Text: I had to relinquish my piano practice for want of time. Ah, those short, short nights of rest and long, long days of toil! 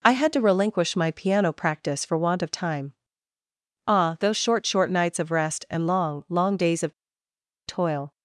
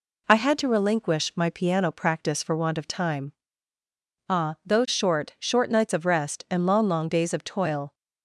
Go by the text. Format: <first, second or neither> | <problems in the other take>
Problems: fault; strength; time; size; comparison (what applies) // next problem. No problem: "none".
second | pauses between "of" and "toil"; noticeable; at 6.9 s; 0.74 s long